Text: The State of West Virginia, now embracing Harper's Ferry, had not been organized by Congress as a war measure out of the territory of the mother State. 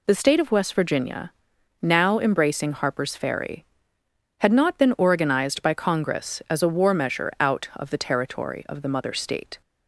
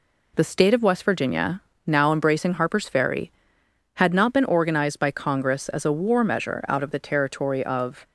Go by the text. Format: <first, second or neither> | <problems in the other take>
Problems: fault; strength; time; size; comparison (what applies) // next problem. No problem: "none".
first | stops before "the mother State"; at 8.0 s